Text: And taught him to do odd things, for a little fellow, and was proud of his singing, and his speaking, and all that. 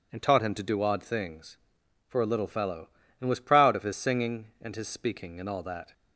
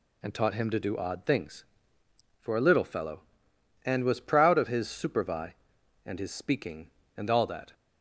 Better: first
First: none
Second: says "supervi" for "singing"; at 4.8 s

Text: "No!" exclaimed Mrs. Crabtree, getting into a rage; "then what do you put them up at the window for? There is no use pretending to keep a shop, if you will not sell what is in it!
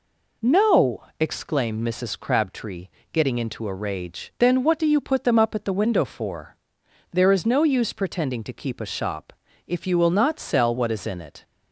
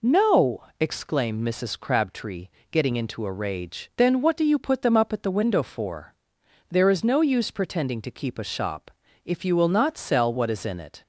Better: neither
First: none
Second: none

